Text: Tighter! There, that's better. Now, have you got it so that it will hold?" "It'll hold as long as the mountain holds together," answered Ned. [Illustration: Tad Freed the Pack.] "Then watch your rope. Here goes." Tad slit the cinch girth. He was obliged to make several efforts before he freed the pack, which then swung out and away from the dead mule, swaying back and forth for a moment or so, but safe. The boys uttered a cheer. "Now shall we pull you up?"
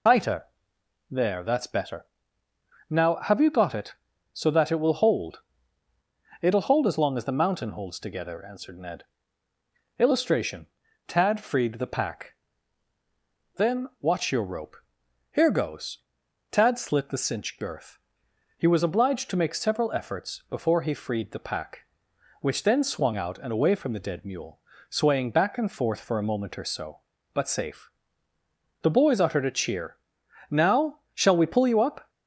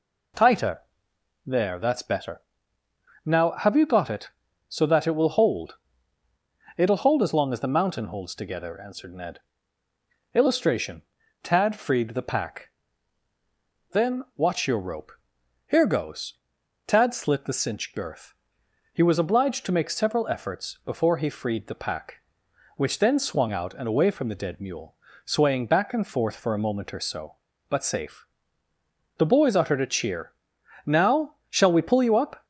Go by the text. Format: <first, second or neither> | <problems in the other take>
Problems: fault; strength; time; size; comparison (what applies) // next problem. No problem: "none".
second | loses the start of "Tighter"; at 0.0 s; 60 ms